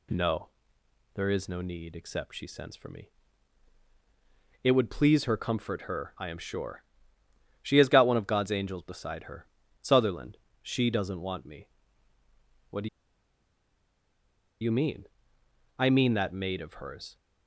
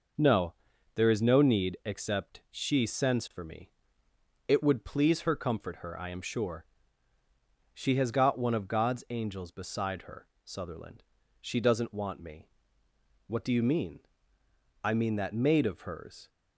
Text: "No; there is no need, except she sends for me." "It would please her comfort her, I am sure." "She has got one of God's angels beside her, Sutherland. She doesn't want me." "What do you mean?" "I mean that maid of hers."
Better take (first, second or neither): second